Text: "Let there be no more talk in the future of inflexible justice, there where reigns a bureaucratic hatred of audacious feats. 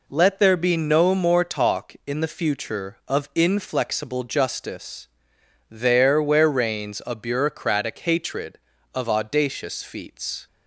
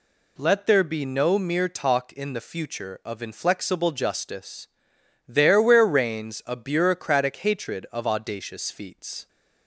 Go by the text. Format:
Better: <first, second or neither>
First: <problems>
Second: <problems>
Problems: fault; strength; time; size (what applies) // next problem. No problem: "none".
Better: first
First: none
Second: says "mere" for "more"; at 1.3 s